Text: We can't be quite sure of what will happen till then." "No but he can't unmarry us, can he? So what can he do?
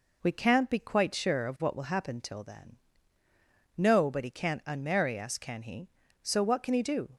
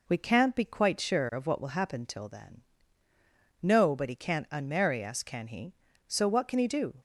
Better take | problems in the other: neither | none

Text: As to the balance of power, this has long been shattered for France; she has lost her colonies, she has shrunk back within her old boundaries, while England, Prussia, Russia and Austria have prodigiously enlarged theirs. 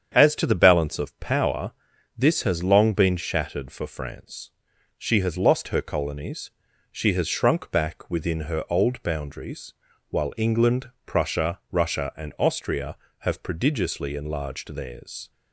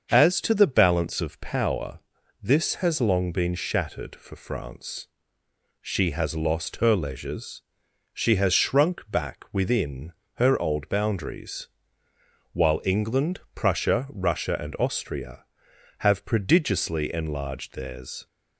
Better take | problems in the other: first | starts louder than the rest; until 1.1 s; 6.5 dB; strong in the first // says "leisures" for "colonies"; at 6.9 s // pauses between "within" and "her"; slight; at 10.1 s; 0.22 s long

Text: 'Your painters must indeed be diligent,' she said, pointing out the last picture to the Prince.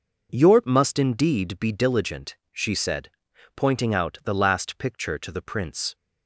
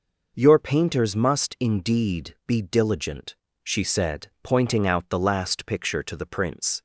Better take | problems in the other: second | skips "painters"; at 0.6 s

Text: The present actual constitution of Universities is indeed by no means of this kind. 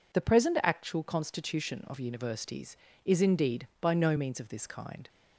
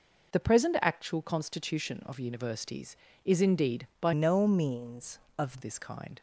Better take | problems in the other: first | changes voice from "no" to "of"; from 4.1 to 5.6 s; 1.5 s long

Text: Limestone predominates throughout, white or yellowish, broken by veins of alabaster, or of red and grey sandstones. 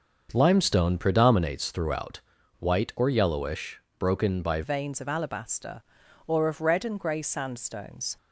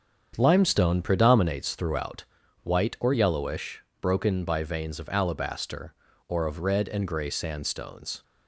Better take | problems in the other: second | starts louder than the rest; until 1.3 s; 6.5 dB; strong in the second // changes voice at "veins"; from 4.6 s on; 3.5 s long

